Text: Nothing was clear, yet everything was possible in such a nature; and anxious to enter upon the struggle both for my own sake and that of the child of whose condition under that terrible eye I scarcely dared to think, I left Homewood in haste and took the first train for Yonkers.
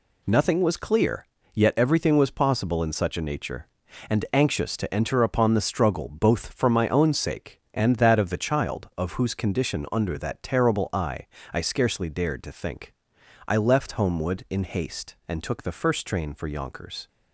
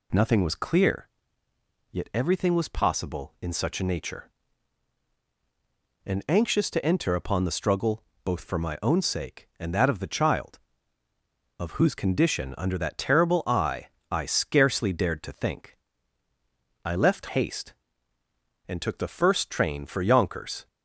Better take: first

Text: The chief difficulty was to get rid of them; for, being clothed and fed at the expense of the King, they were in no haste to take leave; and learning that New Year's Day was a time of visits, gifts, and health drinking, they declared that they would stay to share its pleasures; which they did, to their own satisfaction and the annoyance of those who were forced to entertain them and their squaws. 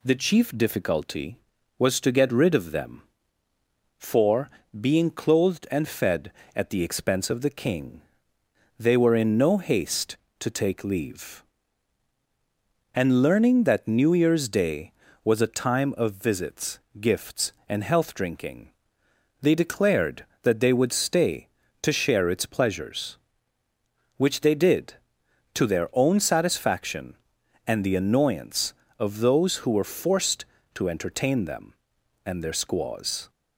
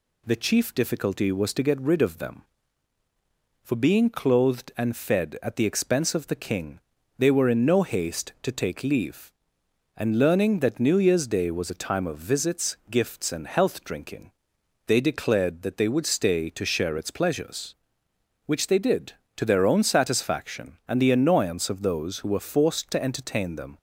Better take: first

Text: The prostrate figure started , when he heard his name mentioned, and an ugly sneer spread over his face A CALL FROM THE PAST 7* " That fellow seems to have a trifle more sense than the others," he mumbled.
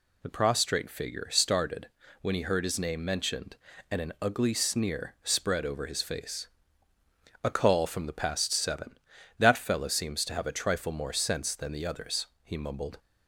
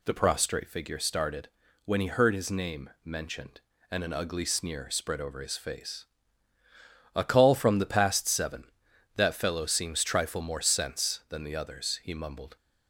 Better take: first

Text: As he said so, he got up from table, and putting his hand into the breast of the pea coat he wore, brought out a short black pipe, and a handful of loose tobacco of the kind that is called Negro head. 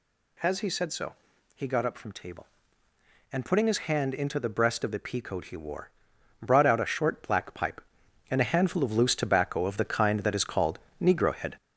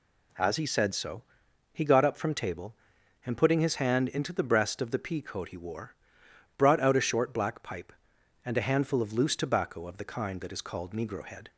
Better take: second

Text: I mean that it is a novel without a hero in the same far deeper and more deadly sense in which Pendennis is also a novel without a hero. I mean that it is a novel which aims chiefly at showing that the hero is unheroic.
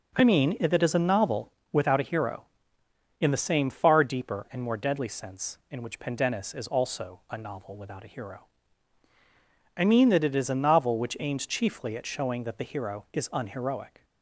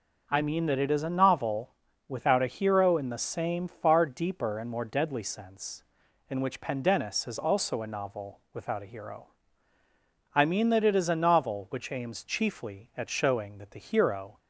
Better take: first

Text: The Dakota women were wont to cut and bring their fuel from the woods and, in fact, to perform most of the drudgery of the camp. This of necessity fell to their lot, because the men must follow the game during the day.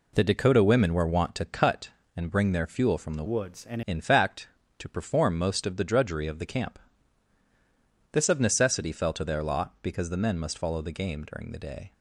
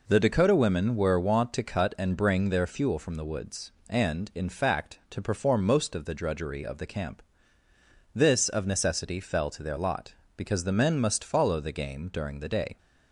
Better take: second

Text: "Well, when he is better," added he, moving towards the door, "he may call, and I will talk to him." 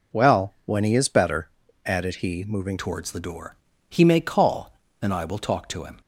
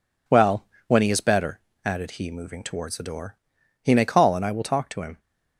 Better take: second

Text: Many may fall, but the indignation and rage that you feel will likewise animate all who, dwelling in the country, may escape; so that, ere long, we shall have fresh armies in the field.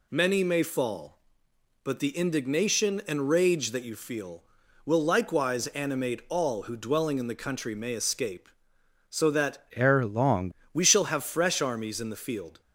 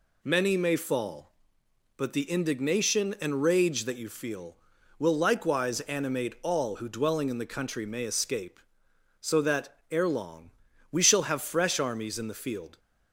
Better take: second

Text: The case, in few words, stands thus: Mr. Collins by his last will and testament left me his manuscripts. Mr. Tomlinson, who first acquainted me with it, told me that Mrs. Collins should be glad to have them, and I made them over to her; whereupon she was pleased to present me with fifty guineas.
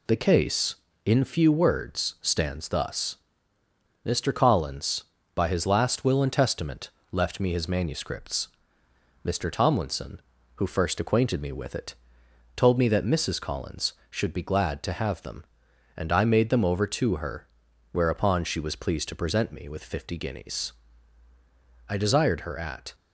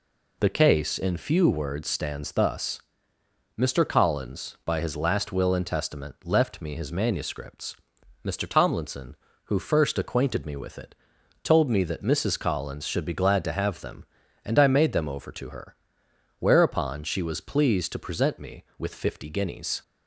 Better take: second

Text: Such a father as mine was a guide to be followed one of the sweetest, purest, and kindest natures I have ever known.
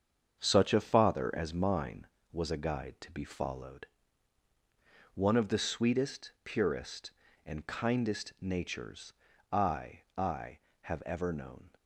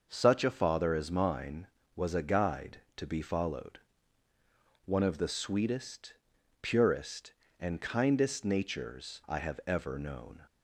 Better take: second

